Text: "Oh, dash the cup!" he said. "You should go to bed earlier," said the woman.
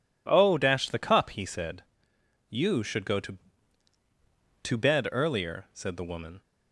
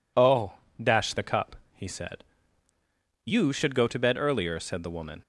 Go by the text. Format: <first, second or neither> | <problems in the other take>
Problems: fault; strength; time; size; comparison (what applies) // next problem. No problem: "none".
second | says "to" twice; at 4.6 s